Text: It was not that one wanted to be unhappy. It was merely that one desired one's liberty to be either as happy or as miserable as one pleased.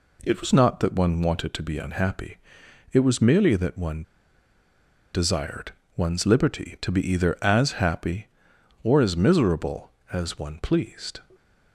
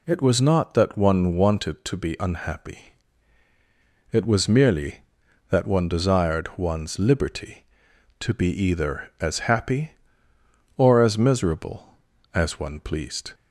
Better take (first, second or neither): second